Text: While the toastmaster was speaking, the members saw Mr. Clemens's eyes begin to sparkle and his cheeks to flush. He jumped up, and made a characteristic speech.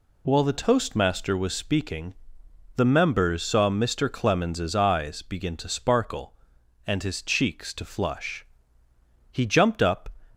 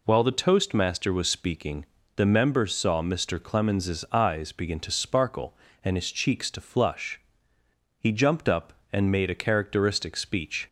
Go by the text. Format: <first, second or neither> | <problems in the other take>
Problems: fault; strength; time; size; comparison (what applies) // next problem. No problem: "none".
second | stops before "and made a characteristic speech"; at 10.3 s